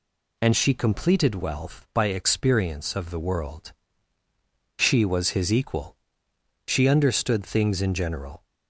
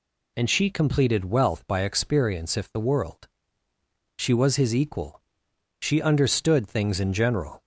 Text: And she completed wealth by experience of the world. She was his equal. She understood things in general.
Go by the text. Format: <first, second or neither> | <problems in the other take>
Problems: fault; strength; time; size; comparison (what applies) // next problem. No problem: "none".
first | says "if" for "of"; at 2.5 s